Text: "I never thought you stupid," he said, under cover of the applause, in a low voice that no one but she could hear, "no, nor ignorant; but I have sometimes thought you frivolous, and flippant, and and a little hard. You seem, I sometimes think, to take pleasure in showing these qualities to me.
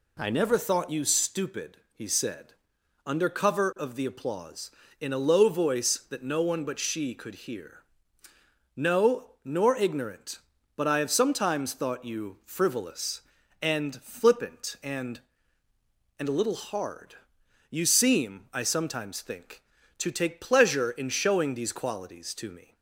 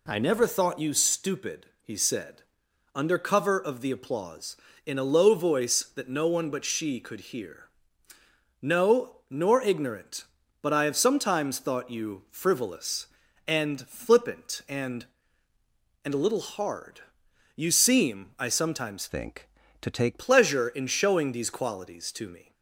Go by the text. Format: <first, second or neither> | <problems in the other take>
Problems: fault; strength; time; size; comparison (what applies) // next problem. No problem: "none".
first | changes voice from "think" to "take"; from 19.0 to 20.2 s; 1.2 s long